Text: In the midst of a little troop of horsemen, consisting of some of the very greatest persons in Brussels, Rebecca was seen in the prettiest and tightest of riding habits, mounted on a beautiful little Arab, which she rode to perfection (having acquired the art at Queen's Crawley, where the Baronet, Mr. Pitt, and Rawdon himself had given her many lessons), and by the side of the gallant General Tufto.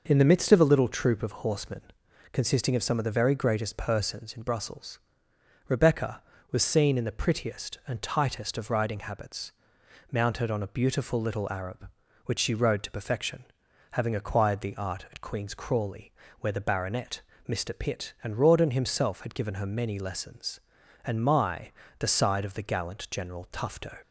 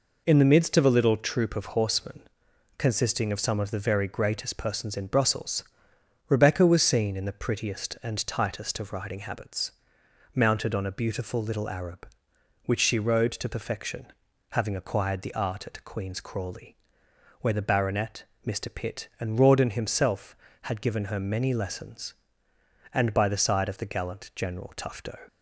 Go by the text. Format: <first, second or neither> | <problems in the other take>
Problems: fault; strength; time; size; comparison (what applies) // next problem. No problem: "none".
second | says "my" for "by"; at 21.2 s